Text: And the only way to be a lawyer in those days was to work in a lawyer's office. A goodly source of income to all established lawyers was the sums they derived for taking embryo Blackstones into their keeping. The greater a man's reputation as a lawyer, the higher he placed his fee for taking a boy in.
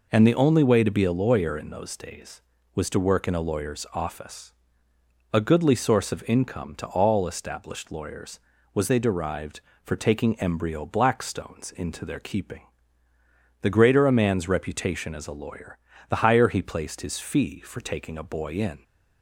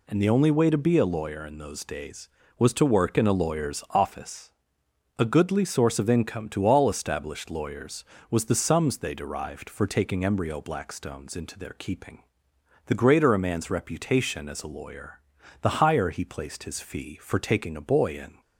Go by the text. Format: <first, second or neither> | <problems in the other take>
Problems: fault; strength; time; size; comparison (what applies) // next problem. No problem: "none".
second | skips "the sums"; at 8.8 s